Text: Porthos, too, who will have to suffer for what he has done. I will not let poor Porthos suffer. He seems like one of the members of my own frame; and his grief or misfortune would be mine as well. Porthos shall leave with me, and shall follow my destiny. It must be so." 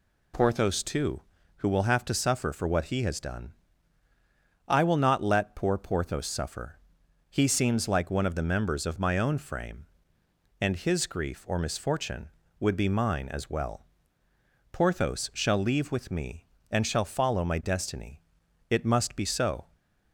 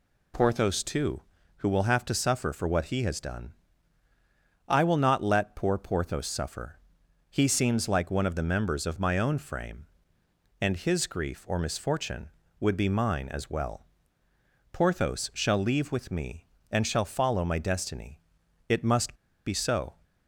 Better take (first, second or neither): first